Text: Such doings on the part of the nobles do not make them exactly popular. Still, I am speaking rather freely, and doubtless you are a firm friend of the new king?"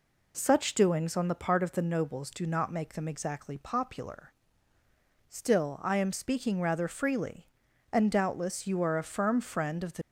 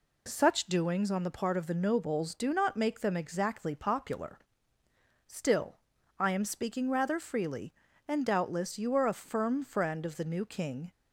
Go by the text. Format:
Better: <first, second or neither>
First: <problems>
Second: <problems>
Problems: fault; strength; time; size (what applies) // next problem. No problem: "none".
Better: second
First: stops before "new king"; at 10.0 s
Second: none